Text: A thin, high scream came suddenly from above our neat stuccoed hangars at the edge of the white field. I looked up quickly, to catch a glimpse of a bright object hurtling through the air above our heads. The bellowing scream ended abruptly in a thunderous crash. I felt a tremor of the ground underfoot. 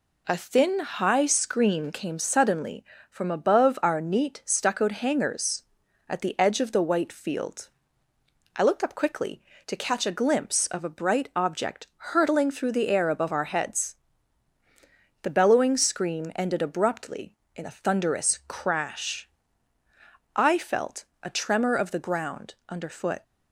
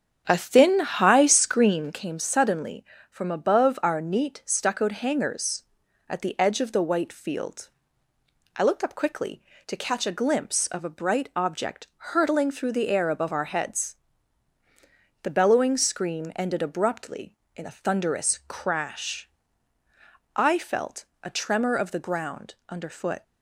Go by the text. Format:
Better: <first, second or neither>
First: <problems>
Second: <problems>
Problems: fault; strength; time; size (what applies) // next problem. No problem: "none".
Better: first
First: pauses between "felt" and "a"; slight; at 21.0 s; 0.18 s long // pauses between "ground" and "underfoot"; slight; at 22.5 s; 0.16 s long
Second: starts louder than the rest; strong; until 1.8 s; 8 dB // pauses between "felt" and "a"; slight; at 21.0 s; 0.18 s long // pauses between "ground" and "underfoot"; slight; at 22.5 s; 0.16 s long